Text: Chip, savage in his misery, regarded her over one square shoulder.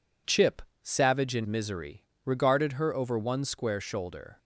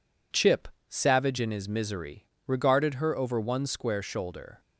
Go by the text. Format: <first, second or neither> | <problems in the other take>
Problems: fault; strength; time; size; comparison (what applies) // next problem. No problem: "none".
second | skips "his"; at 1.4 s